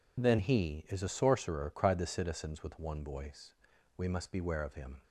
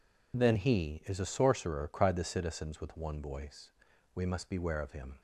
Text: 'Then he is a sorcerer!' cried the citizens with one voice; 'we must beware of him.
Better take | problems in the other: neither | none

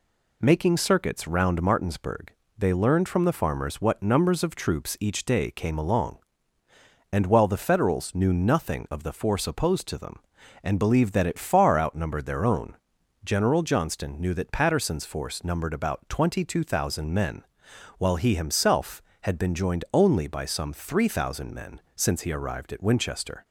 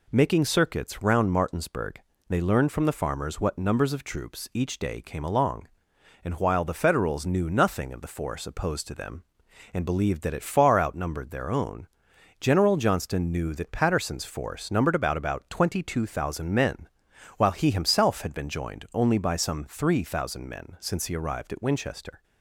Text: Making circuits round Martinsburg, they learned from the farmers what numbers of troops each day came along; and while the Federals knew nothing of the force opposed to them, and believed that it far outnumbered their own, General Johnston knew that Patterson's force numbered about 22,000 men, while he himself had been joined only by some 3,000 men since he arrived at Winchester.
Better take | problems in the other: first | says "about" twice; at 15.1 s

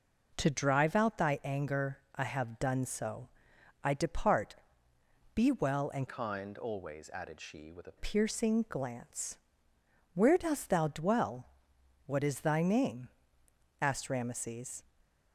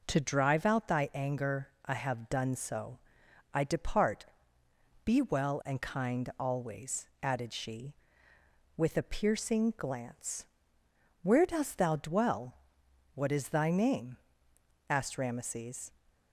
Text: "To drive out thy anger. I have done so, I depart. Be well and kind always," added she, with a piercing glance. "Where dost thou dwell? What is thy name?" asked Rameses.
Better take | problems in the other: second | changes voice from "kind" to "a"; from 6.0 to 7.9 s; 1.9 s long

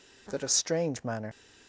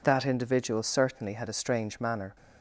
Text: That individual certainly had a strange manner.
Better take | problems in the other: second | skips "individual certainly had"; at 0.4 s

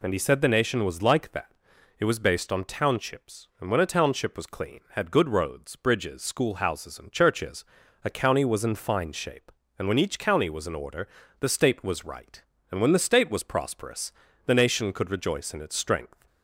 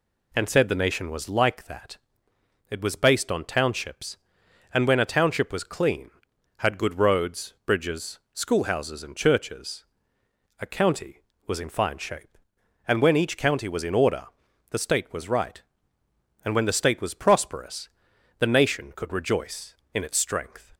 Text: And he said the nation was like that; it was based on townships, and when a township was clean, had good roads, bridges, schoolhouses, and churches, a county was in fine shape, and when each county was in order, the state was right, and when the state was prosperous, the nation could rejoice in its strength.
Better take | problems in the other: first | skips "he"; at 0.4 s

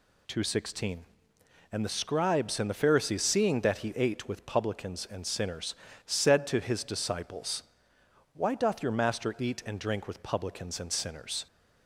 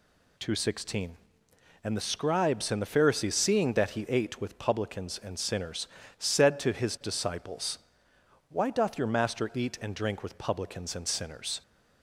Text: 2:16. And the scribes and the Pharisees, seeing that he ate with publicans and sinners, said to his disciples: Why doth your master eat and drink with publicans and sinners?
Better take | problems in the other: neither | none

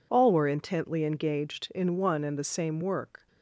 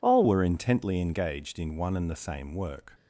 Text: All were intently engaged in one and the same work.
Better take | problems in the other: first | changes voice at "were"; from 0.2 s on; 2.7 s long

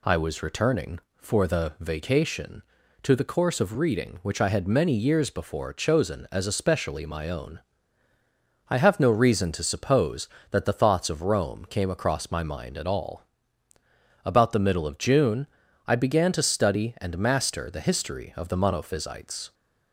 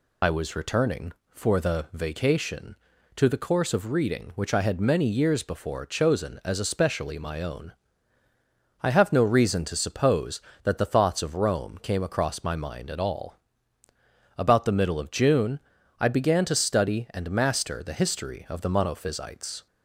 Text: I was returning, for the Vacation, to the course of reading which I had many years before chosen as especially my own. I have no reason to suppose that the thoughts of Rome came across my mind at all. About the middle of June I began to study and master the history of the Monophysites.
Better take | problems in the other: first | loses the start of "I"; at 0.2 s; 60 ms // pauses between "June" and "I"; at 15.5 s; 0.42 s long; also in the first

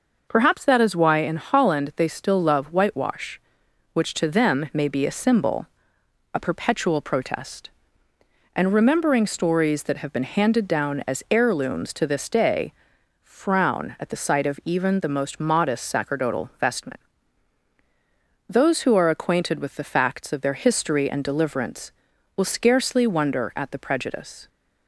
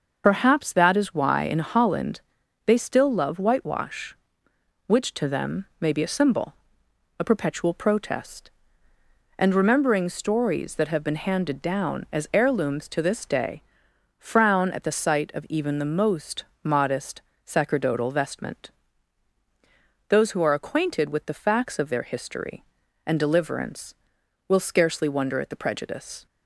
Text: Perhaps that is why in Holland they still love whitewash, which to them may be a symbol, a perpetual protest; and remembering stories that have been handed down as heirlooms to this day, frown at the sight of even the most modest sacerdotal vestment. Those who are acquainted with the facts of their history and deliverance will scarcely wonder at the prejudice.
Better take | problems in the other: first | loses the start of "Perhaps"; at 0.2 s; 50 ms // starts louder than the rest; until 1.2 s; 6 dB // pauses between "Holland" and "they"; at 2.2 s; 0.44 s long // pauses between "most" and "modest"; slight; at 16.4 s; 0.18 s long // pauses between "modest" and "sacerdotal"; slight; at 17.2 s; 0.24 s long

